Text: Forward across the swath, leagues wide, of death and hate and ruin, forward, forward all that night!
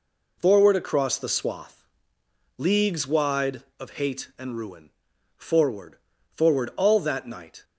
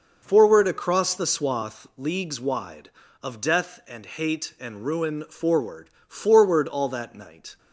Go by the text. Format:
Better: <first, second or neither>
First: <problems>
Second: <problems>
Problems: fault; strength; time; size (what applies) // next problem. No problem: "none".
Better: second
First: skips "death and"; at 3.9 s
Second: none